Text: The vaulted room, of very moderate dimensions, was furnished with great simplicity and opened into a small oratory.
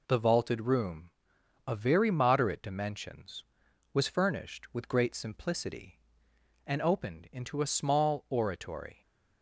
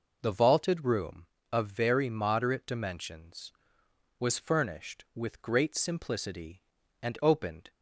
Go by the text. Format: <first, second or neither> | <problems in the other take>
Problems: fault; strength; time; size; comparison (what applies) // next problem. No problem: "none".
first | stops before "into a small oratory"; at 7.6 s